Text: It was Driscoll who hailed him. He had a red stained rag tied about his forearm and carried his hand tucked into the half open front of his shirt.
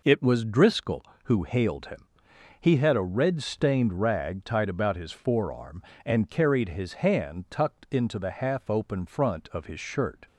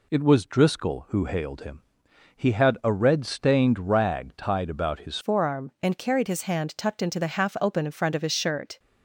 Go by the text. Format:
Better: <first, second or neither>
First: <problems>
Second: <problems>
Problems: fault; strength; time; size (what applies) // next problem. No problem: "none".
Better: first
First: none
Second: changes voice at "forearm"; from 5.2 s on; 3.5 s long